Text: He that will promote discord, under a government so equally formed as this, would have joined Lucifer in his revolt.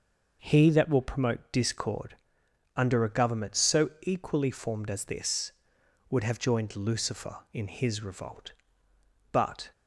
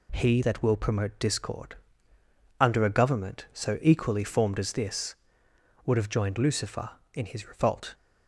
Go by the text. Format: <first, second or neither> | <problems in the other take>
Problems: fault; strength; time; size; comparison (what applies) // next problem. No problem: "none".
second | goes on to say "But"; slight; from 9.3 s on; 0.38 s long